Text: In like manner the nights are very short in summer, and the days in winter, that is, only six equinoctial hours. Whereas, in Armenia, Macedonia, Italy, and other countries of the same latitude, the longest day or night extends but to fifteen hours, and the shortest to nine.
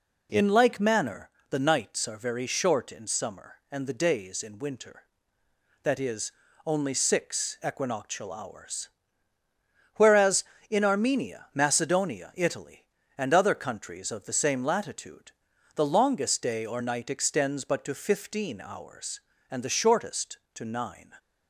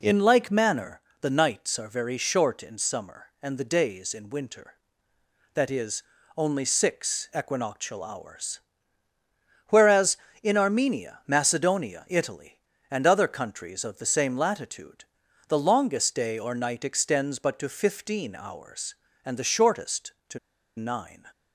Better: first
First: pauses between "manner" and "the"; slight; at 1.2 s; 0.22 s long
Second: pauses between "manner" and "the"; slight; at 0.9 s; 0.22 s long // pauses between "to" and "nine"; at 20.3 s; 0.39 s long

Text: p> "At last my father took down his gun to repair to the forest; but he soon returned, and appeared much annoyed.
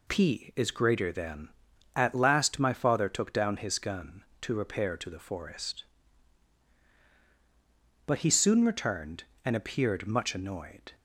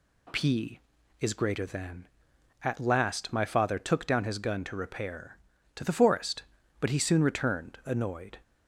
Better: first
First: none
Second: skips "and appeared much"; at 7.8 s

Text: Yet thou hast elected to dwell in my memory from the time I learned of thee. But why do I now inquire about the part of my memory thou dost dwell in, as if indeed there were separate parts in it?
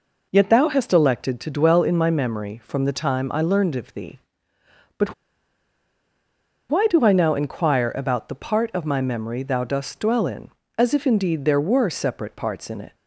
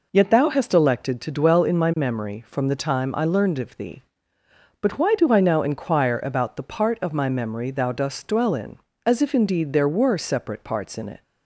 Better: second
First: pauses between "But" and "why"; strong; at 5.1 s; 1.5 s long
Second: none

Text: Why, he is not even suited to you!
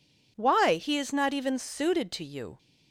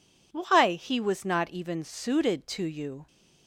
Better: first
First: none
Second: says "was" for "is"; at 1.0 s

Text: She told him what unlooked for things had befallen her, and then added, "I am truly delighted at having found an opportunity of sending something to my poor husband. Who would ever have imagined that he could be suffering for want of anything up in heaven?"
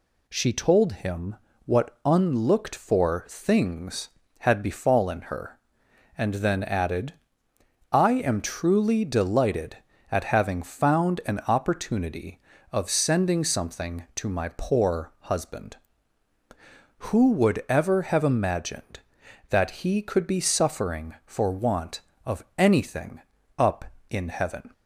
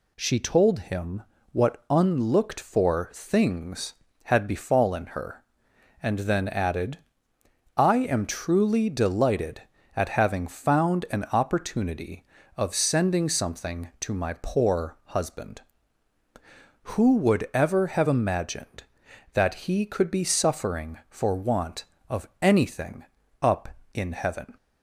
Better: neither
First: pauses between "him" and "what"; slight; at 1.3 s; 0.30 s long // pauses between "of" and "anything"; slight; at 22.4 s; 0.16 s long // pauses between "anything" and "up"; at 23.2 s; 0.38 s long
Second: pauses between "him" and "what"; slight; at 1.2 s; 0.30 s long // pauses between "of" and "anything"; slight; at 22.2 s; 0.16 s long // pauses between "anything" and "up"; at 23.0 s; 0.38 s long

